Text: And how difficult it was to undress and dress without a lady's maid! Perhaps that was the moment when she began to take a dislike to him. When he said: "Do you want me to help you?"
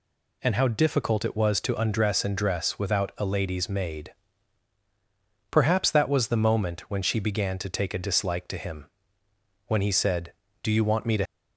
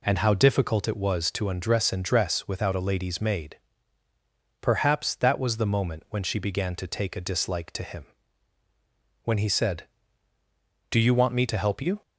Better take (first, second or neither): second